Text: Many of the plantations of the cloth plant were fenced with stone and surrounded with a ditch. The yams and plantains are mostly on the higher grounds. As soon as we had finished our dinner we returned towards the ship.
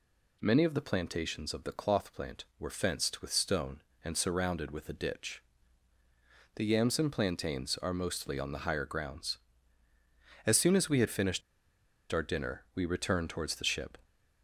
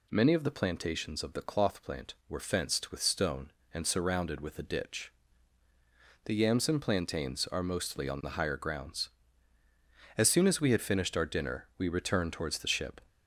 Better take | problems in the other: second | pauses between "finished" and "our"; noticeable; at 11.4 s; 0.71 s long

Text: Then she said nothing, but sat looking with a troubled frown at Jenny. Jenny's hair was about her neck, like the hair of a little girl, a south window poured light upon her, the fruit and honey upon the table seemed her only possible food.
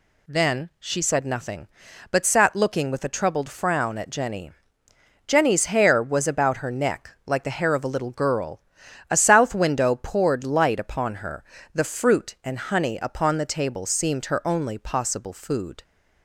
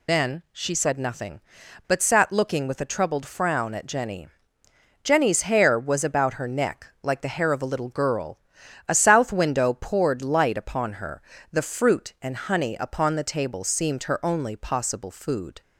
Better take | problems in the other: first | loses the start of "Then"; at 0.0 s; 85 ms

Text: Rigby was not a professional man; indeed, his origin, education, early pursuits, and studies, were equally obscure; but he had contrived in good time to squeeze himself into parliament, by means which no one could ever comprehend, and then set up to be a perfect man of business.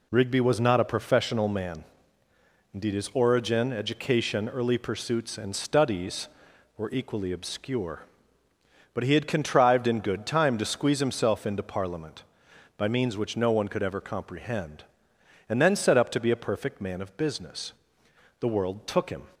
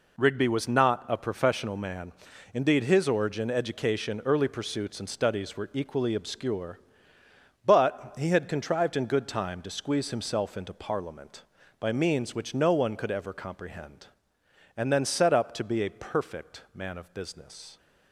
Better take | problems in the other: second | goes on to say "The world took him"; noticeable; from 18.3 s on; 0.88 s long

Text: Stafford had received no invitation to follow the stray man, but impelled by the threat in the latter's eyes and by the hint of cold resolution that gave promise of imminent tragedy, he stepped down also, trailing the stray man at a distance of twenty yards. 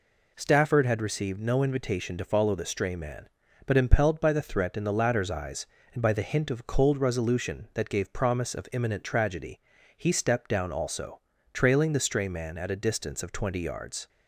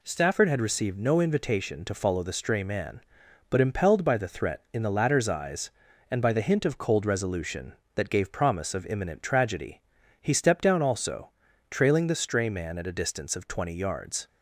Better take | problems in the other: neither | none

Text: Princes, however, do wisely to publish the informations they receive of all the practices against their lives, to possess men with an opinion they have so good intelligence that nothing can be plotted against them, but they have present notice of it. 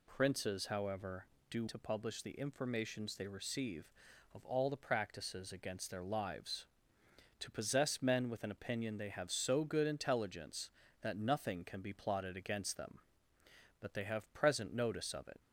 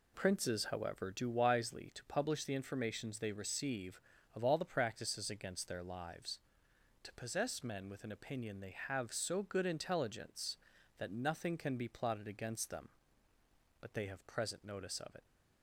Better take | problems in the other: second | skips "wisely"; at 1.6 s

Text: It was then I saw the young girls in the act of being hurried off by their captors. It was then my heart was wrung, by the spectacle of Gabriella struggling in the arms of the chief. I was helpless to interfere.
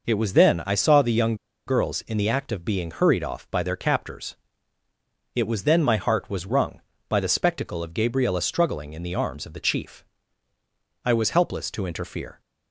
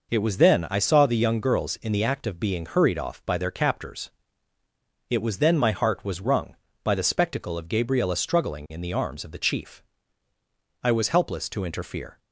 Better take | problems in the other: second | pauses between "young" and "girls"; slight; at 1.3 s; 0.32 s long

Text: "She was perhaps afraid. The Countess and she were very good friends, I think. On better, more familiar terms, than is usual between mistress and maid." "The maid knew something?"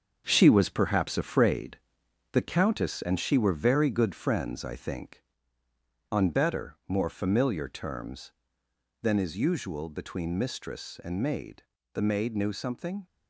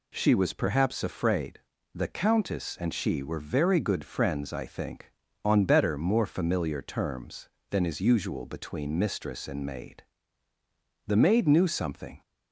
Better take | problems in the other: second | gets quieter; throughout; 7 dB

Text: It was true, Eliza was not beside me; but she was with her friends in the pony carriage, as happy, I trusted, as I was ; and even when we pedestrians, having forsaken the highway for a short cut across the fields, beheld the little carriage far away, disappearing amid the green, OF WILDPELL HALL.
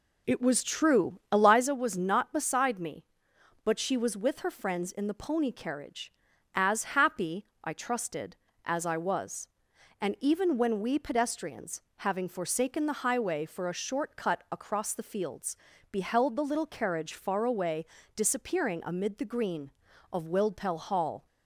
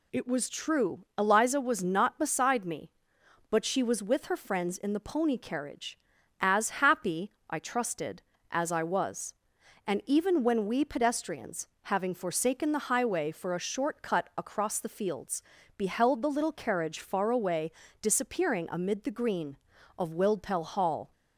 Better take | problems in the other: second | starts louder than the rest; slight; until 1.7 s; 3 dB

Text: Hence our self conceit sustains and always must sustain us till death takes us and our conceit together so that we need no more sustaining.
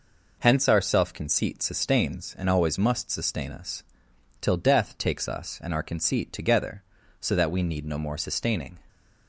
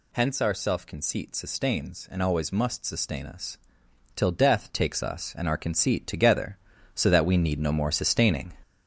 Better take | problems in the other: first | gets louder; noticeable; throughout; 5.5 dB // pauses between "us" and "till"; noticeable; at 3.5 s; 0.58 s long; noticeable in the first

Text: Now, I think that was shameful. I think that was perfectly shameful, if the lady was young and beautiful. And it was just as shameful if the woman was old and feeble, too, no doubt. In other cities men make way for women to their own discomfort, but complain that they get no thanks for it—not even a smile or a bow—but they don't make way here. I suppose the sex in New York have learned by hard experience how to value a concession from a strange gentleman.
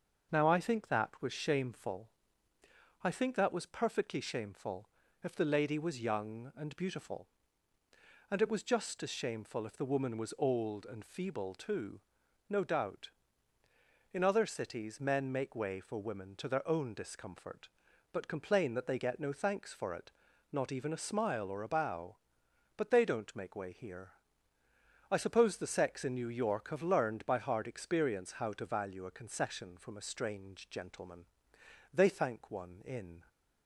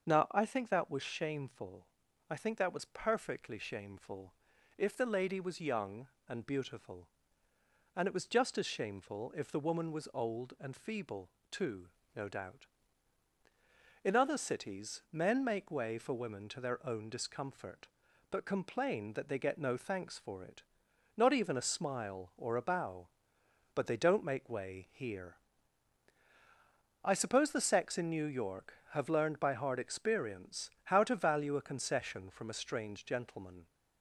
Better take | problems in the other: second | starts louder than the rest; until 1.3 s; 6.5 dB; also in the second // goes on to say "They thank one in"; from 31.9 s on; 1.3 s long

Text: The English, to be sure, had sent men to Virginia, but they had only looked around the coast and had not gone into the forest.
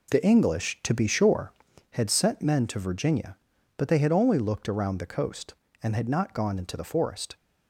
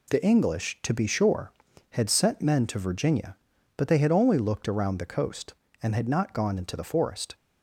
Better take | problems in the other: second | starts louder than the rest; until 1.8 s; 3.5 dB

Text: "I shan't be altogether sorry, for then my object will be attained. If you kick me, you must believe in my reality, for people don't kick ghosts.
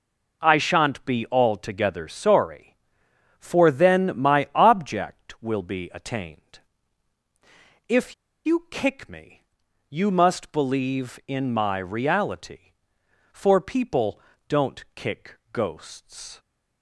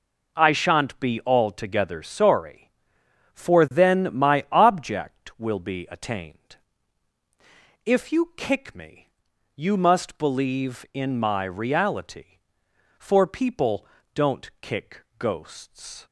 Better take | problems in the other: second | pauses between "If" and "you"; slight; at 8.1 s; 0.31 s long // pauses between "people" and "don't"; slight; at 14.1 s; 0.28 s long; slight in the second

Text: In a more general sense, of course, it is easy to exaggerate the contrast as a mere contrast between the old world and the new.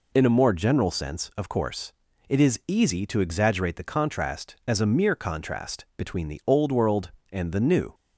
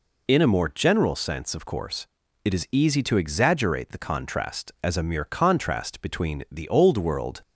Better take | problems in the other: first | stops before "and the new"; at 7.4 s

